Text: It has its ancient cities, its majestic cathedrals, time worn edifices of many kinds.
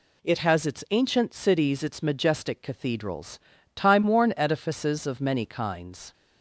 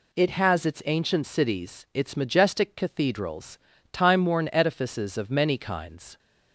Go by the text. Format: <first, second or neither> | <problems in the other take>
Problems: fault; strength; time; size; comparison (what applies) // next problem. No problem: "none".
neither | none